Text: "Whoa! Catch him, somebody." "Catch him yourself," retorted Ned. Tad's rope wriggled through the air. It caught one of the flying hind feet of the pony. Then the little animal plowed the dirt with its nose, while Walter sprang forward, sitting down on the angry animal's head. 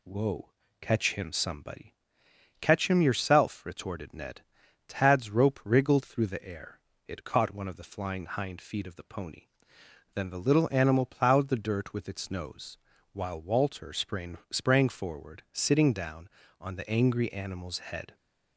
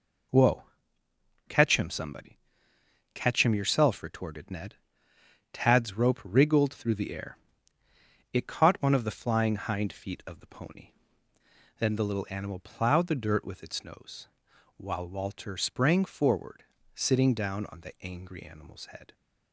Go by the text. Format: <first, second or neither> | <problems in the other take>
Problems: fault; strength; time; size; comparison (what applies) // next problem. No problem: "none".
second | says "sprang" twice; at 14.4 s